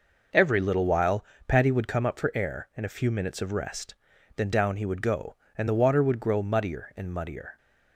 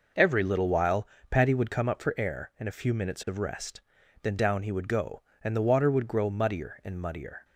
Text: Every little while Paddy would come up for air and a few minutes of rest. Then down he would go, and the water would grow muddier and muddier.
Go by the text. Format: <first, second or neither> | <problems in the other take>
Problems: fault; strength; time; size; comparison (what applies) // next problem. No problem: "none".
neither | pauses between "while" and "Paddy"; slight; the same in both